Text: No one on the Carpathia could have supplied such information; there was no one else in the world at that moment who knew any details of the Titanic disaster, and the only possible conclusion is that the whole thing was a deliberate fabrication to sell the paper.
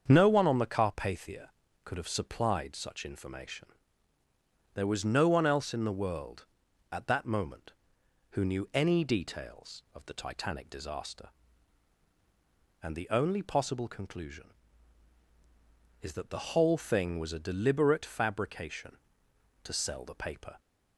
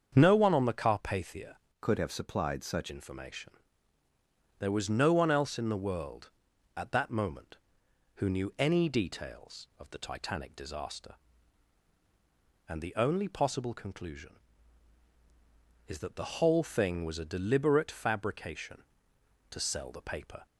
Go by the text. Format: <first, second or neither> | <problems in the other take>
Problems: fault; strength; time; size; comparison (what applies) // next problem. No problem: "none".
first | starts louder than the rest; strong; until 1.1 s; 7 dB; strong in the first // changes voice from "could" to "such"; from 1.7 to 2.9 s; 1.2 s long